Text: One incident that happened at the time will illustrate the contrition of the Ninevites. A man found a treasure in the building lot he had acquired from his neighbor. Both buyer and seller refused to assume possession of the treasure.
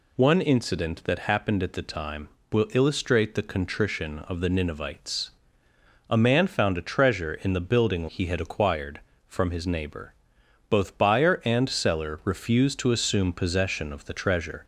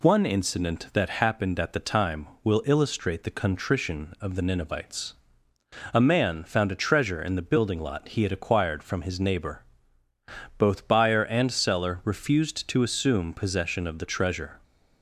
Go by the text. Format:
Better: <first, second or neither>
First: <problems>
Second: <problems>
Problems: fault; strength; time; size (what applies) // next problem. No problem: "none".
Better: second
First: skips "lot"; at 8.0 s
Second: none